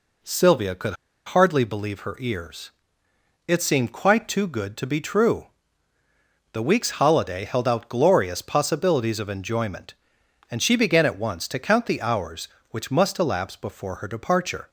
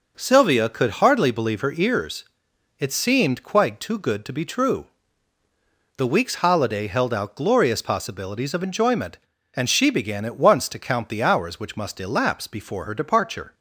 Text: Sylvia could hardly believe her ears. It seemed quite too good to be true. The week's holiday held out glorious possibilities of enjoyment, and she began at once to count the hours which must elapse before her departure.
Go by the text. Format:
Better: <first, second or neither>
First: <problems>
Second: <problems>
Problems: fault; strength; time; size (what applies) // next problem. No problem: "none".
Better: second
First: pauses between "could" and "hardly"; slight; at 0.9 s; 0.31 s long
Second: none